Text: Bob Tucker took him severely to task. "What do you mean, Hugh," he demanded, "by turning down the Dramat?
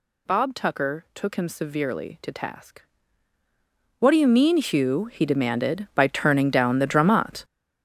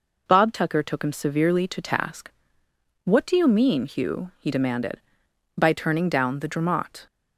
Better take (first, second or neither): second